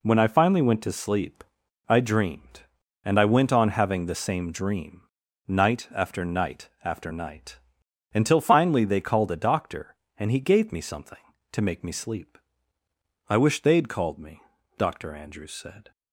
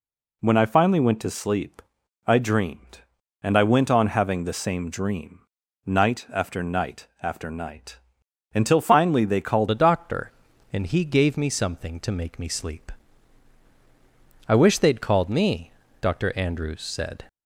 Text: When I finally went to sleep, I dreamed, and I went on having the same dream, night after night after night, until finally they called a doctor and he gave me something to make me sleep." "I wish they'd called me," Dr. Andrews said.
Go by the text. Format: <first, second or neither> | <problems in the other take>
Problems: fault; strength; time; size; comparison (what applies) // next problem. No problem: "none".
first | pauses between "night" and "after"; slight; at 7.0 s; 0.16 s long; slight in the first // changes voice at "a"; from 9.7 s on; 7.5 s long